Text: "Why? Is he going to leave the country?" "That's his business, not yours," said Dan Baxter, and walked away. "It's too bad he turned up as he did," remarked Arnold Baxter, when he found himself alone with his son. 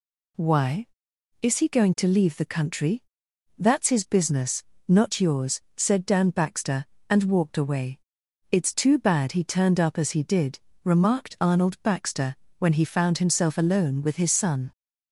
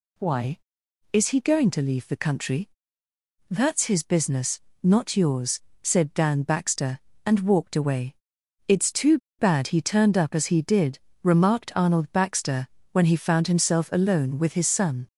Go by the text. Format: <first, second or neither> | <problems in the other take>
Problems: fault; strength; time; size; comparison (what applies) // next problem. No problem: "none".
first | pauses between "too" and "bad"; slight; at 9.1 s; 0.20 s long